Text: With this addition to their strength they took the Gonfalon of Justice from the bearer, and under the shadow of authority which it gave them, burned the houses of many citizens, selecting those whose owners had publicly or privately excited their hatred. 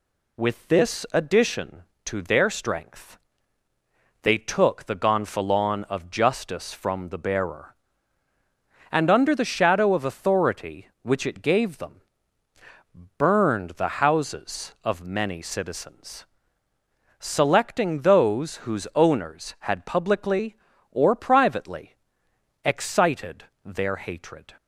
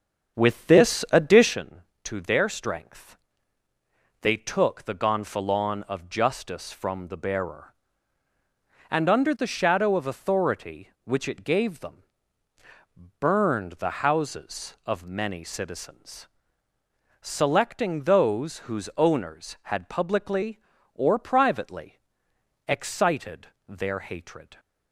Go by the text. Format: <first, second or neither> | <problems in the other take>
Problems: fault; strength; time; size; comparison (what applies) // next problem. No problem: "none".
first | starts louder than the rest; strong; until 1.6 s; 7.5 dB // pauses between "strength" and "they"; at 3.1 s; 1.0 s long; also in the first // pauses between "privately" and "excited"; noticeable; at 21.9 s; 0.68 s long; noticeable in the first // pauses between "excited" and "their"; slight; at 23.4 s; 0.20 s long; slight in the first